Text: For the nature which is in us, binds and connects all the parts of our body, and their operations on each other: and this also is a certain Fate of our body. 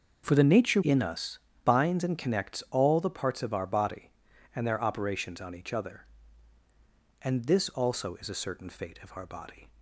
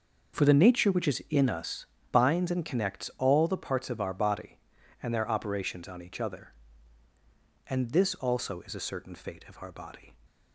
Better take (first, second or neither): second